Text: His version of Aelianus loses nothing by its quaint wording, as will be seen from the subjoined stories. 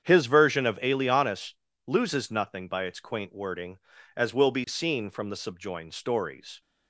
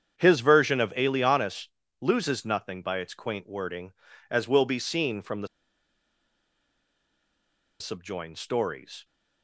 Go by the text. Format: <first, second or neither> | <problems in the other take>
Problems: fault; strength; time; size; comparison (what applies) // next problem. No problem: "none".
first | starts louder than the rest; strong; until 1.1 s; 8 dB; strong in the first // pauses between "Aelianus" and "loses"; slight; at 1.6 s; 0.32 s long; slight in the first // pauses between "the" and "subjoined"; strong; at 5.4 s; 2.3 s long